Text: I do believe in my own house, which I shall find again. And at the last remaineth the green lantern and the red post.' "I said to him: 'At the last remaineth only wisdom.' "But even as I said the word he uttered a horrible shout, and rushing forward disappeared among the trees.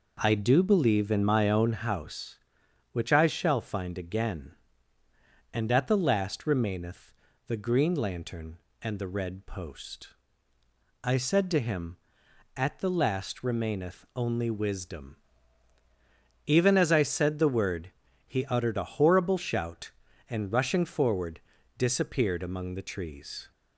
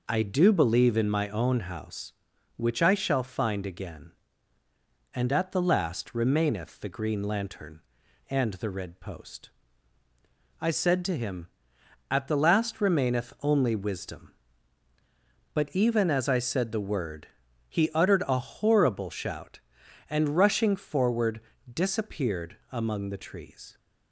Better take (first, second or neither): second